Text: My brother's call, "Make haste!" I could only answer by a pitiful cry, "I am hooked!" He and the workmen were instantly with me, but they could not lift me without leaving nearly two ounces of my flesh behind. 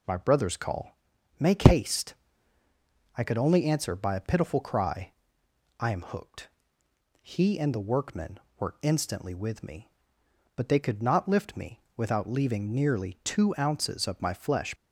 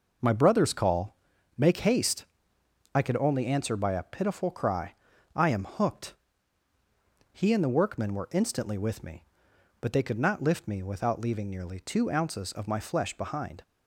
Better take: second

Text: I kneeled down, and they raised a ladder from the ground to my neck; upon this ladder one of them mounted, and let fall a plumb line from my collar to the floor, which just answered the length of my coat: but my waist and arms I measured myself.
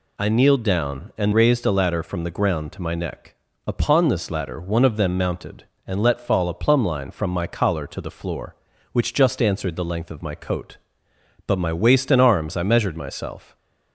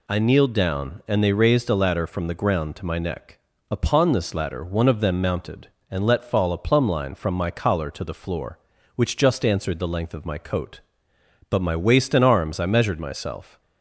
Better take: second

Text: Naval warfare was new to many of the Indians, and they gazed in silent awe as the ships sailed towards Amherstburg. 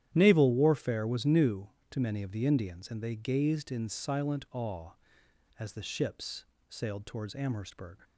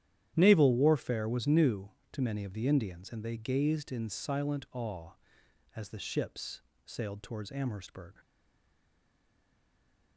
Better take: first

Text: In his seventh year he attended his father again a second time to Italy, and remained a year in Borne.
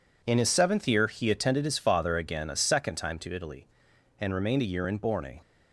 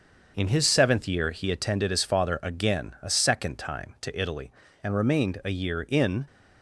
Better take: first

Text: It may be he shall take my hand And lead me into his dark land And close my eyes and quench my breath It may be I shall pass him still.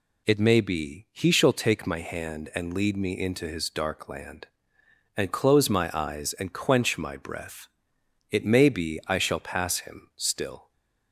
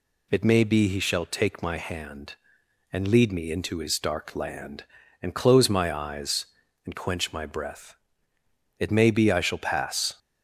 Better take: first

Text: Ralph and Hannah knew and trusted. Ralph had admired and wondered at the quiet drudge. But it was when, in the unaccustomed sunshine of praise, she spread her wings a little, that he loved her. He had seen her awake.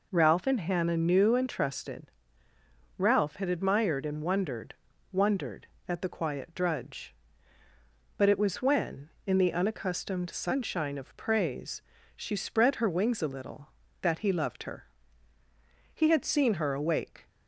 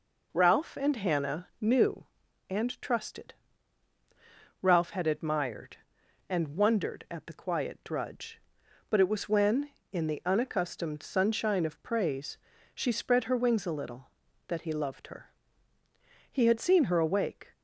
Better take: second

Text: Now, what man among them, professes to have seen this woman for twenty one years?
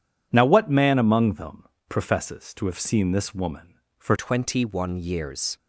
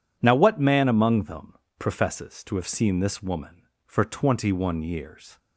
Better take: second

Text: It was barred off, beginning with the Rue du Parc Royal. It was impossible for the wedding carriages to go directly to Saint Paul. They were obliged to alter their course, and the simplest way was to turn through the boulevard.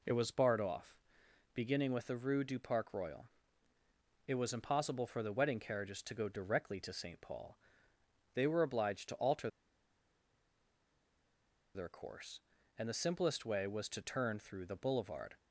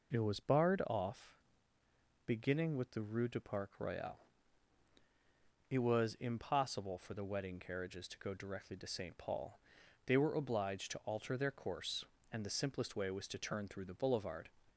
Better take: second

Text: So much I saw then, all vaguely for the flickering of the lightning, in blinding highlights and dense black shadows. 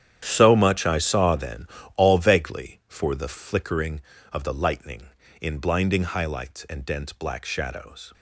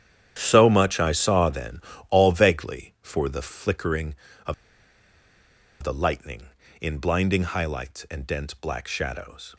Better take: first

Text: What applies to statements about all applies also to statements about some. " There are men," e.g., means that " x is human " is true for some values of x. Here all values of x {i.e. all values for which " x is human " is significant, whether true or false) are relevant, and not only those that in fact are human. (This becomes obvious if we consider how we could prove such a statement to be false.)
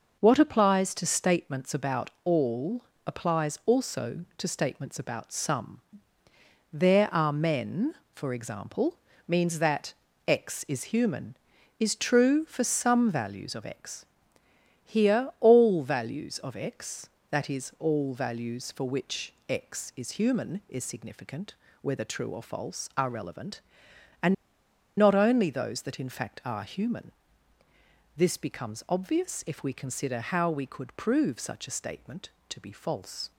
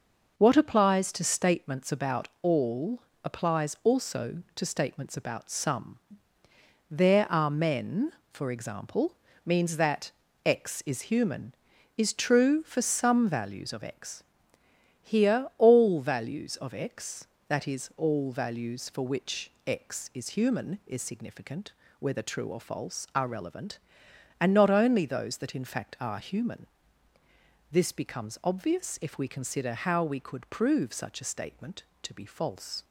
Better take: second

